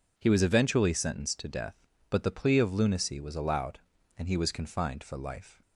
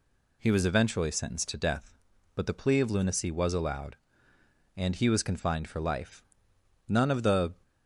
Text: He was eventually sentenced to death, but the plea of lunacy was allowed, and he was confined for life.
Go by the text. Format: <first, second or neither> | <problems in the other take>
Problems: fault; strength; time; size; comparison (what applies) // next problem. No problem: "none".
first | goes on to say "None of the"; noticeable; from 6.8 s on; 0.64 s long